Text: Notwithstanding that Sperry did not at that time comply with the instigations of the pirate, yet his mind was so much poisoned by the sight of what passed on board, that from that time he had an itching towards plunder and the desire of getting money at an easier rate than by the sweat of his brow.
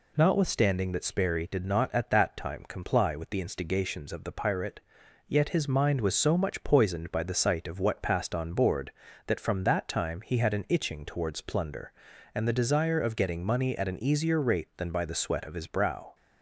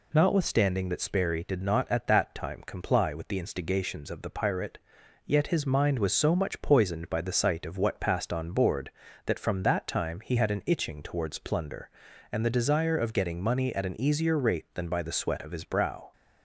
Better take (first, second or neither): neither